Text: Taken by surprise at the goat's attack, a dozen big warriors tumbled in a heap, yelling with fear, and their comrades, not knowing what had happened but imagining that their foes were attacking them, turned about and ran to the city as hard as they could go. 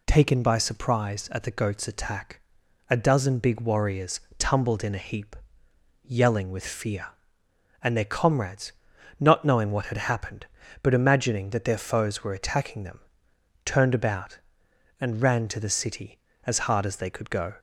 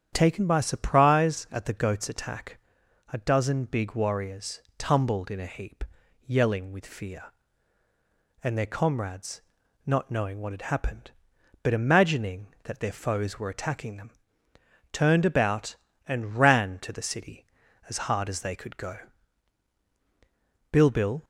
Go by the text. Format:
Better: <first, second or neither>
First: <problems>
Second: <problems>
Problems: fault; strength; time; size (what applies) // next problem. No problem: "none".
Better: first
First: pauses between "warriors" and "tumbled"; slight; at 4.1 s; 0.18 s long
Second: starts louder than the rest; strong; until 1.1 s; 9 dB // pauses between "warriors" and "tumbled"; slight; at 4.6 s; 0.16 s long // goes on to say "Bilbil"; from 20.7 s on; 0.52 s long